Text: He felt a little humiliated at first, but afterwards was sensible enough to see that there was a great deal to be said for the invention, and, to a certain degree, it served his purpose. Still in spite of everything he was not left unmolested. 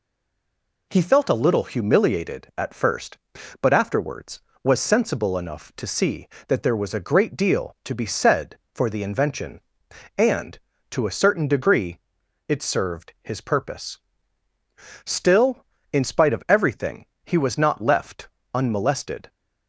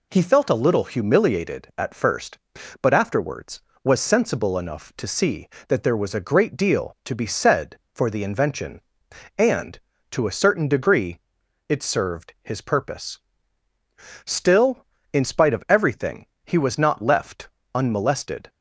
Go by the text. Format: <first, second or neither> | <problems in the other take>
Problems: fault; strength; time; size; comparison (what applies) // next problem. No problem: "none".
second | stays silent before the first word; slight; until 0.9 s; 0.9 s long // pauses between "everything" and "he"; slight; at 17.0 s; 0.18 s long; slight in the second // pauses between "left" and "unmolested"; slight; at 18.2 s; 0.26 s long; slight in the second